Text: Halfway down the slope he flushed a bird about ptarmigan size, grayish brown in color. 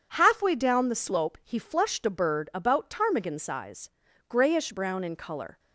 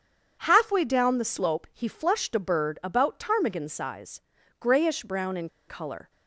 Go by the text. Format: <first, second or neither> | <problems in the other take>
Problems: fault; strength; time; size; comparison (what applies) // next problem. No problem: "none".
first | starts louder than the rest; strong; until 1.4 s; 7.5 dB // pauses between "in" and "color"; slight; at 5.4 s; 0.19 s long